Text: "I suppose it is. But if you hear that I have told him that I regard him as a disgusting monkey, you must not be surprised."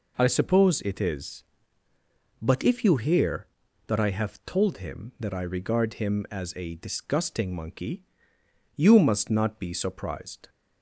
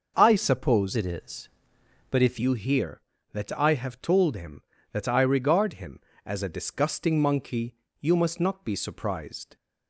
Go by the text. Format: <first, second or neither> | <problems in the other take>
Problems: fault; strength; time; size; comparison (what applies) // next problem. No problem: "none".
first | changes voice from "it" to "if"; from 0.9 to 2.3 s; 1.4 s long